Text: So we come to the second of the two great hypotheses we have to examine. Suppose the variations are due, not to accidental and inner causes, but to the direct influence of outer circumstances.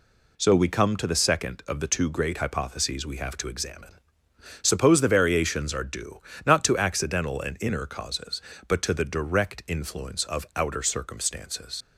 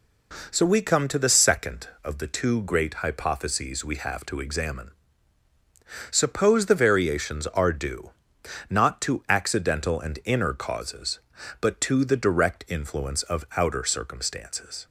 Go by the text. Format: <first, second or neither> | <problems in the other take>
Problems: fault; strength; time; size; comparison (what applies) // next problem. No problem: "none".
second | leaves "circumstances" unfinished; at 11.8 s; 125 ms